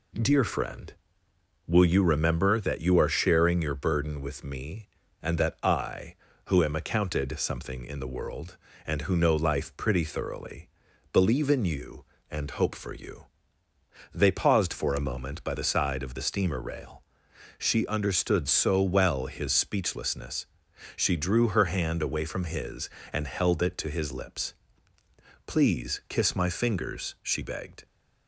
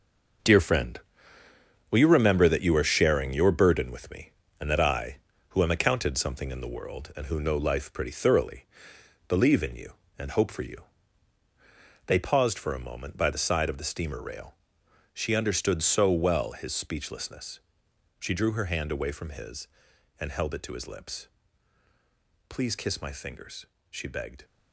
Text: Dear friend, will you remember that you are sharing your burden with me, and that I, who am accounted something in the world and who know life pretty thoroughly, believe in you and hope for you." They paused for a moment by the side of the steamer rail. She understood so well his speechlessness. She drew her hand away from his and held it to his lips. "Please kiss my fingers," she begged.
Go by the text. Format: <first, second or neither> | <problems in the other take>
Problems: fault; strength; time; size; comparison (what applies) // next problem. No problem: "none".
first | gets quieter; strong; throughout; 9 dB